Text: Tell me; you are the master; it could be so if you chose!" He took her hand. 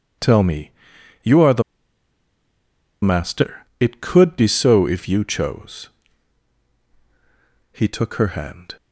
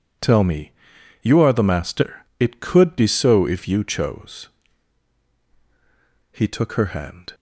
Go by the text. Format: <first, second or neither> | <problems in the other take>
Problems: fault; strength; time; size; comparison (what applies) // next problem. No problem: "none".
second | pauses between "the" and "master"; strong; at 1.6 s; 1.4 s long